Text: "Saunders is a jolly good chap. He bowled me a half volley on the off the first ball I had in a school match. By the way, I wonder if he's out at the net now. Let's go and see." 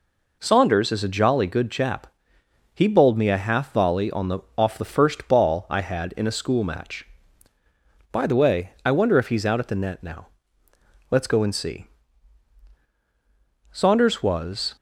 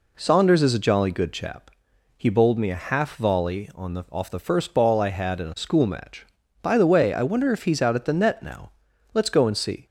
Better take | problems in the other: second | pauses between "the" and "off"; slight; at 4.3 s; 0.18 s long // goes on to say "Saunders was"; noticeable; from 13.7 s on; 1.0 s long

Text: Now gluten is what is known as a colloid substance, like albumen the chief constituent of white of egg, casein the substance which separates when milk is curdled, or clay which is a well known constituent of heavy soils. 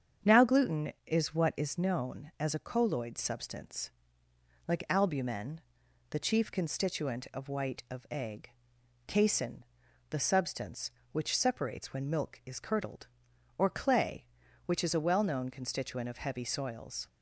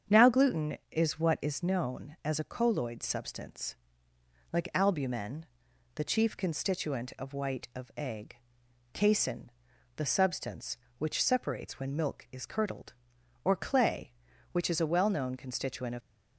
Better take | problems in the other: first | starts louder than the rest; strong; until 1.2 s; 7.5 dB; strong in the first // pauses between "albumen" and "the"; noticeable; at 5.4 s; 0.52 s long; noticeable in the first // pauses between "casein" and "the"; noticeable; at 9.4 s; 0.46 s long; noticeable in the first // stops before "heavy soils"; at 16.0 s

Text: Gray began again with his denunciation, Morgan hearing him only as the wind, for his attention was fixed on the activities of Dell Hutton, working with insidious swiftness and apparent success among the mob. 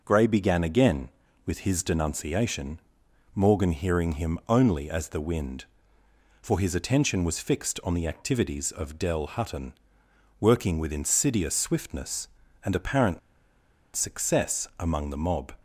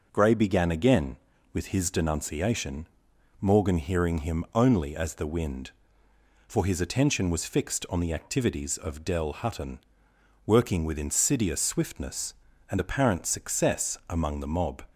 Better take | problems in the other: second | pauses between "apparent" and "success"; noticeable; at 13.1 s; 0.76 s long

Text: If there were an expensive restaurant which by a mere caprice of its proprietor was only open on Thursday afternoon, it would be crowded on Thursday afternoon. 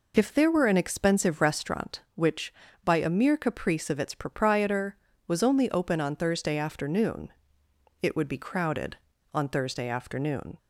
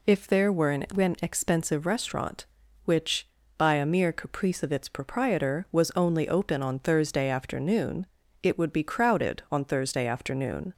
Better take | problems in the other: first | says "an" twice; at 0.9 s

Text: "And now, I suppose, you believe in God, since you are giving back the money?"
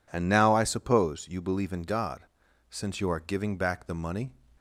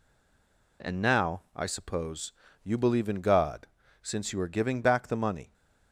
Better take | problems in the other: first | stays silent before the first word; slight; until 0.8 s; 0.8 s long

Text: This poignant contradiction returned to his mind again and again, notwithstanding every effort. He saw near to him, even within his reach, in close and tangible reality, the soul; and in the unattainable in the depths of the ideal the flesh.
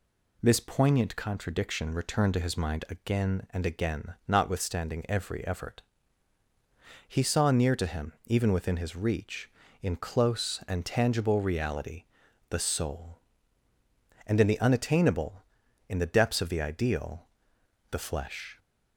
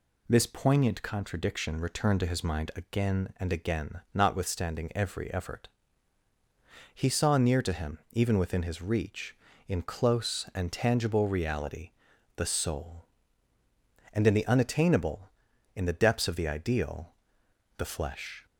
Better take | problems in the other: neither | pauses between "ideal" and "the"; noticeable; the same in both

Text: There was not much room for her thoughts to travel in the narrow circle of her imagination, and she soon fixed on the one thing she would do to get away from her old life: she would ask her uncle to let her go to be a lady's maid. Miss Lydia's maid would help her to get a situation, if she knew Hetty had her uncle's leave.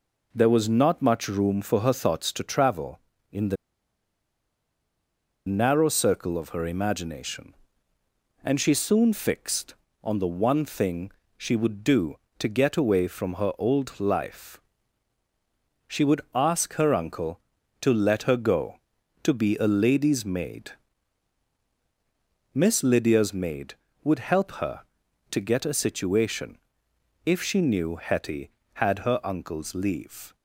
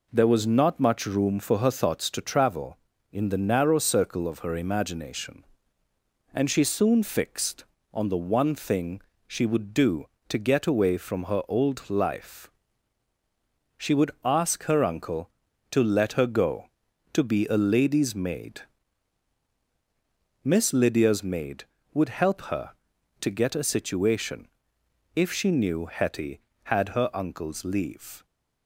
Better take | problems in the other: second | pauses between "the" and "narrow"; strong; at 3.5 s; 1.9 s long // pauses between "thing" and "she"; slight; at 11.1 s; 0.26 s long; slight in the second

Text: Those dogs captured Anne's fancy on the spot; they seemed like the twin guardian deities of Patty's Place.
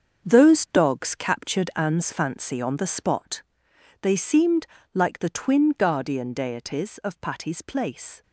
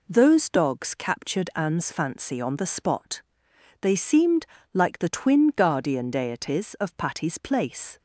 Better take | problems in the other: second | gets quieter; strong; throughout; 11 dB // pauses between "seemed" and "like"; slight; at 4.6 s; 0.26 s long; slight in the second

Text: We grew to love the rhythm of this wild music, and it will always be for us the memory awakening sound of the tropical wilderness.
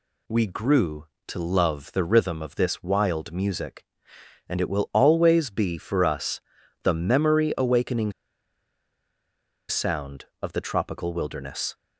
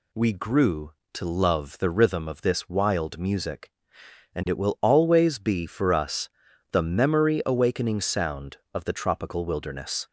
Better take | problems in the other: second | pauses between "us" and "the"; at 6.3 s; 0.42 s long; also in the second // pauses between "awakening" and "sound"; strong; at 8.1 s; 1.5 s long

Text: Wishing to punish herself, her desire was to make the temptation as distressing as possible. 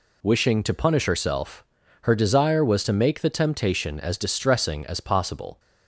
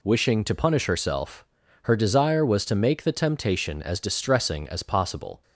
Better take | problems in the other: neither | none

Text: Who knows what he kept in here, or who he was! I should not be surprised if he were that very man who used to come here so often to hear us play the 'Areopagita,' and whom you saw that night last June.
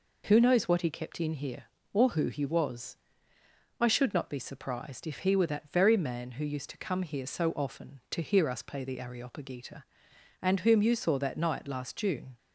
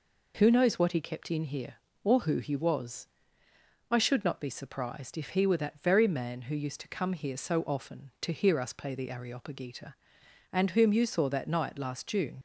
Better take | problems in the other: first | leaves "June" unfinished; at 12.3 s; 65 ms

